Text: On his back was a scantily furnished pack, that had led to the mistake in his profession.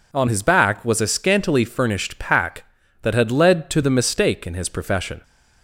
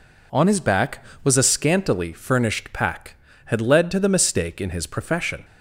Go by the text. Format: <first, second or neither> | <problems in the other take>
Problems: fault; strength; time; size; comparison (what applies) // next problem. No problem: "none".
first | skips "that"; at 3.3 s